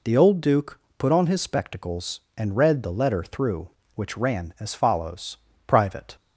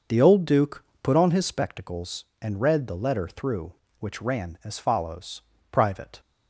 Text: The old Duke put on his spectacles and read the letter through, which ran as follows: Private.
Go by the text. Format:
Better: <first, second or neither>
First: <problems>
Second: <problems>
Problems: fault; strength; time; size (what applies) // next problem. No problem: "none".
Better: first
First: pauses between "Duke" and "put"; slight; at 0.7 s; 0.18 s long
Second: starts louder than the rest; noticeable; until 1.8 s; 6 dB // pauses between "Duke" and "put"; slight; at 0.8 s; 0.18 s long